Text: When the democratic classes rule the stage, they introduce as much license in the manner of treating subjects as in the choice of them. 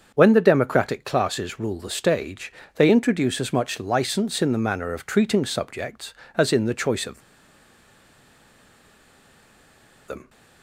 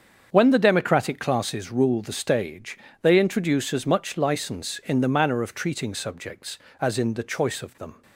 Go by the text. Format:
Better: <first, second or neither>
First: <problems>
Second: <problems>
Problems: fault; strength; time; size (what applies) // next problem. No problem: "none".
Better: second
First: starts louder than the rest; until 1.1 s; 6.5 dB // pauses between "of" and "them"; strong; at 7.2 s; 2.8 s long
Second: starts louder than the rest; until 1.3 s; 7 dB